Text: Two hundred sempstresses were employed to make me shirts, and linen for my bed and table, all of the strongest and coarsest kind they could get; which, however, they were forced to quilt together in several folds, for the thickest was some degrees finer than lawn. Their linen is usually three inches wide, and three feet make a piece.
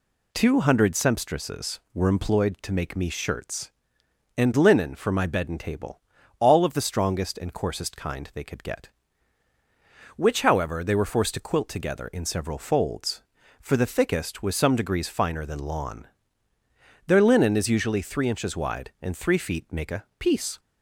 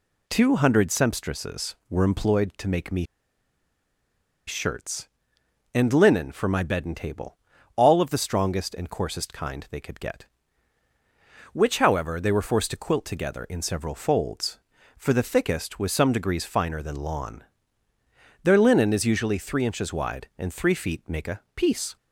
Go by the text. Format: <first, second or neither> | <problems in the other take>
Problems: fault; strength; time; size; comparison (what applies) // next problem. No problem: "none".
first | pauses between "me" and "shirts"; strong; at 3.0 s; 1.4 s long